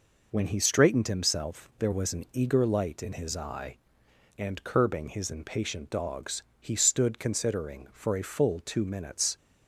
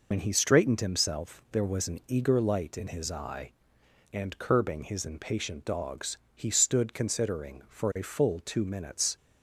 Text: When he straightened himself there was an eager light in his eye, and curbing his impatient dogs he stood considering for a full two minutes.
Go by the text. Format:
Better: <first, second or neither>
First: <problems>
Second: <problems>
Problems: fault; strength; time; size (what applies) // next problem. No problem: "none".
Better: first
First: pauses between "dogs" and "he"; slight; at 6.4 s; 0.20 s long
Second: loses the start of "When"; at 0.1 s; 55 ms // pauses between "dogs" and "he"; slight; at 6.1 s; 0.20 s long